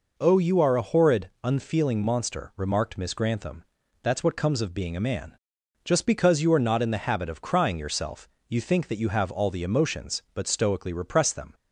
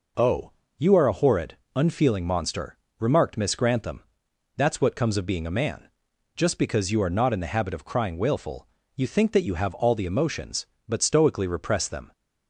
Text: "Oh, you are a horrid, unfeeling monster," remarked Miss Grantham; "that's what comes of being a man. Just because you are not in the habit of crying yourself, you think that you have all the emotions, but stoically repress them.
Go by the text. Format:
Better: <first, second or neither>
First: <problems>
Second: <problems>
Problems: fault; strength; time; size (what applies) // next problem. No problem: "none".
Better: first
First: none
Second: says "wailful" for "yourself"; at 8.1 s